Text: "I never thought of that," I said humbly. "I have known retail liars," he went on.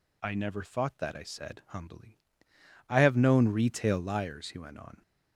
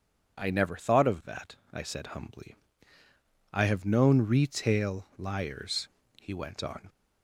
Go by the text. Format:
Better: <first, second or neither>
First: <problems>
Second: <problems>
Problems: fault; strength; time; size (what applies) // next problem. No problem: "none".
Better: second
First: skips "of"; at 0.9 s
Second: none